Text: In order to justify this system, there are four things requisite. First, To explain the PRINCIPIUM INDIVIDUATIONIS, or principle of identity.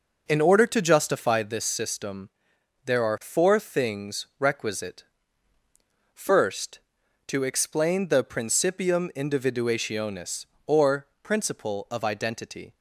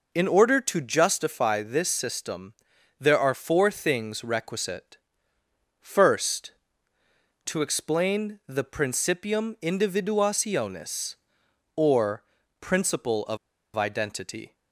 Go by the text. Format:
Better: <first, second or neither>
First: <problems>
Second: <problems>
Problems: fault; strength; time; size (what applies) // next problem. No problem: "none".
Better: first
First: pauses between "or" and "principle"; slight; at 11.0 s; 0.16 s long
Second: pauses between "or" and "principle"; at 12.2 s; 0.38 s long // pauses between "of" and "identity"; at 13.3 s; 0.38 s long